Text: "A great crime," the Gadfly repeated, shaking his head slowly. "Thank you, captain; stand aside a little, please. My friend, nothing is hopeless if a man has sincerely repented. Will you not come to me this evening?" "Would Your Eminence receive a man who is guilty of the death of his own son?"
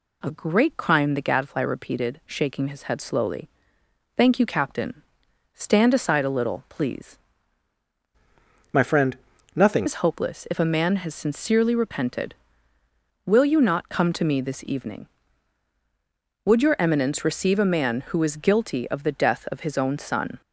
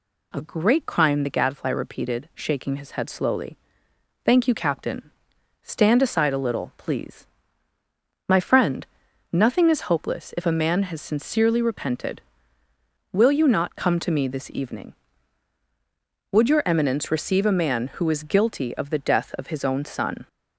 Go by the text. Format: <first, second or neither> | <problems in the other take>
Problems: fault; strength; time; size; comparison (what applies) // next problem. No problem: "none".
second | changes voice from "My" to "nothing"; from 8.7 to 9.8 s; 1.1 s long